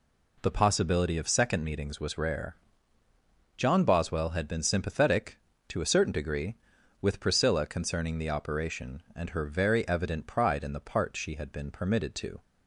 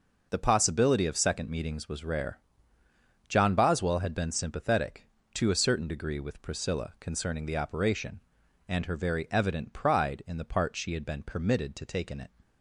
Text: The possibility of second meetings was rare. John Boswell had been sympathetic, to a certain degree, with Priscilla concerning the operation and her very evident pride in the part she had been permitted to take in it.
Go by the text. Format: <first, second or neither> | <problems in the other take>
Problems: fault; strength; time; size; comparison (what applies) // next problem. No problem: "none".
second | stops before "take in it"; at 12.4 s